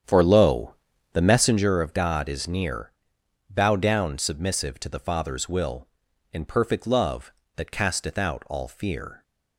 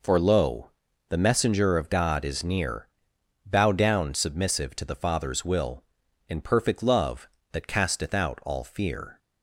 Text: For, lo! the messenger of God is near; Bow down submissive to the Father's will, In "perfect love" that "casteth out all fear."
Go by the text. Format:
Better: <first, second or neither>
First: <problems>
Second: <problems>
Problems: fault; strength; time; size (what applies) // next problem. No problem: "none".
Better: second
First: starts louder than the rest; strong; until 1.7 s; 8.5 dB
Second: none